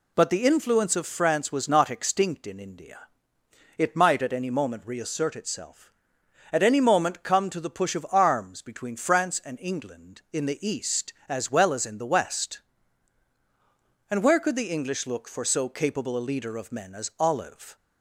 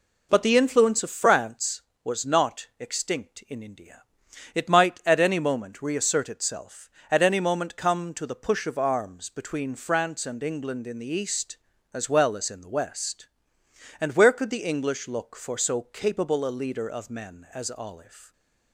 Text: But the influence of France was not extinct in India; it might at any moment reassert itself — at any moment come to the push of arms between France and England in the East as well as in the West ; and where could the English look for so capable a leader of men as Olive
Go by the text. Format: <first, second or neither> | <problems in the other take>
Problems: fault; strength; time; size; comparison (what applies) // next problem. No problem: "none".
neither | none